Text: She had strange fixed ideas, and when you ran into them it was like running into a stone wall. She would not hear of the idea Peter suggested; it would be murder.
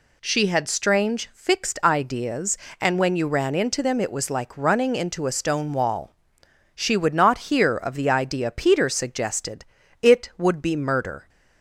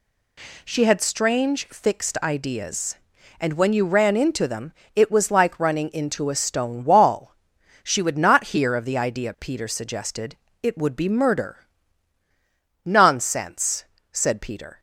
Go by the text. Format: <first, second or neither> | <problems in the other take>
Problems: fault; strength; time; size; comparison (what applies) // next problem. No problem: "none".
first | pauses between "them" and "it"; slight; at 4.7 s; 0.22 s long // goes on to say "Nonsense said Peter"; strong; from 12.8 s on; 1.9 s long